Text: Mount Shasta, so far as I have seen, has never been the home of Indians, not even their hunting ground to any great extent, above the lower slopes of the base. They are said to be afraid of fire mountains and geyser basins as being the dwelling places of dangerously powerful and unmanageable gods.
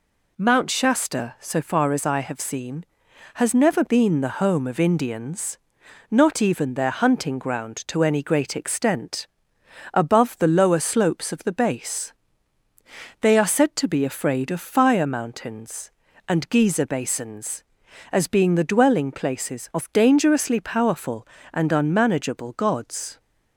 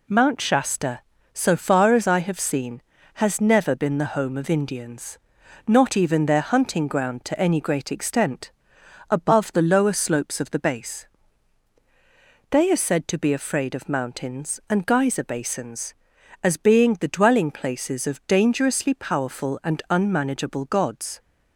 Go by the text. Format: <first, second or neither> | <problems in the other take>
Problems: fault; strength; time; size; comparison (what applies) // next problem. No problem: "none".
first | skips "fire"; at 13.8 s